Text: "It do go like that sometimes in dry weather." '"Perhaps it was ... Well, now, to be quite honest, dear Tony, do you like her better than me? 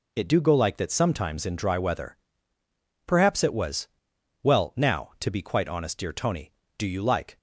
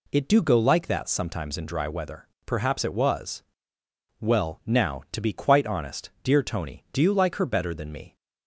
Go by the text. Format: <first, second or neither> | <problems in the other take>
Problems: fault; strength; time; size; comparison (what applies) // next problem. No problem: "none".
second | stops before "her better than me"; at 7.3 s